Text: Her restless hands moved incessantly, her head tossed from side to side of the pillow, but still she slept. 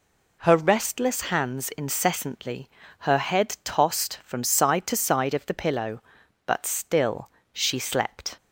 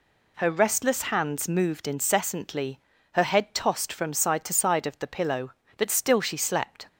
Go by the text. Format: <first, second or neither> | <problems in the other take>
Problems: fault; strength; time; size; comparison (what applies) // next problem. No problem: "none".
second | skips "moved"; at 1.7 s // pauses between "still" and "she"; slight; at 7.3 s; 0.22 s long